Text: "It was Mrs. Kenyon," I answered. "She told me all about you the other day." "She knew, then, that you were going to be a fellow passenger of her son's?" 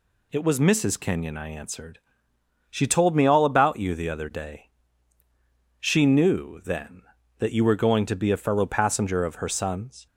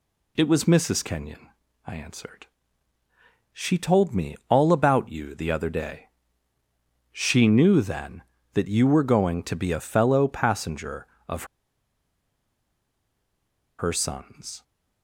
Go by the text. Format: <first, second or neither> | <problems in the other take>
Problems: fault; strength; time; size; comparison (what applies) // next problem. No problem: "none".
first | pauses between "of" and "her"; strong; at 11.4 s; 2.3 s long